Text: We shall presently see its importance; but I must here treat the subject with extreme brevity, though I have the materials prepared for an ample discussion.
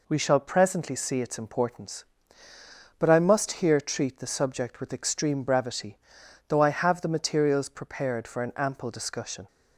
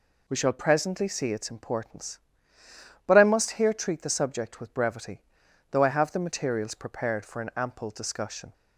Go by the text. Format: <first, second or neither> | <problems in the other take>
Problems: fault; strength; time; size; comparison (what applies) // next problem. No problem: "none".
first | skips "extreme"; at 4.7 s